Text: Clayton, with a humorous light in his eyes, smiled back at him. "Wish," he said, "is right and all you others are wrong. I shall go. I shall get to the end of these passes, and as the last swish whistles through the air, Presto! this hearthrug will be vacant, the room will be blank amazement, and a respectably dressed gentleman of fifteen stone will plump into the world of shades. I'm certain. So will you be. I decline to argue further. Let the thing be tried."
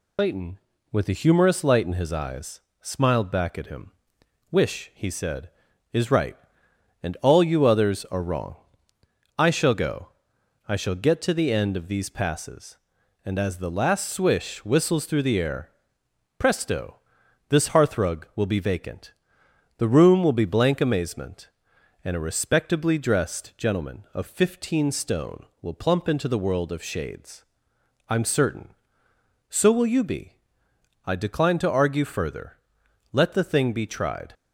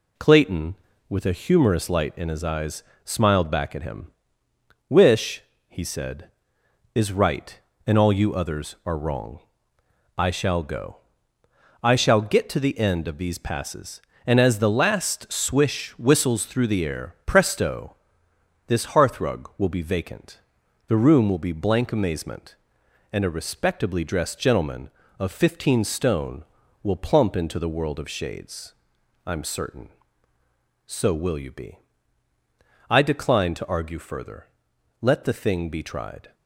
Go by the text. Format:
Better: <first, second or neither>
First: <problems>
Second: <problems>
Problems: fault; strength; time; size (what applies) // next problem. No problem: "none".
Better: second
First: loses the start of "Clayton"; at 0.1 s; 75 ms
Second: none